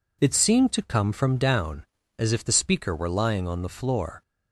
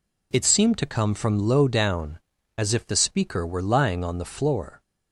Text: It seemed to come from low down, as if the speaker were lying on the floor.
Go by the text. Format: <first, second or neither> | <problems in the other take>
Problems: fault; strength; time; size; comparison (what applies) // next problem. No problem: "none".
second | skips "low"; at 1.3 s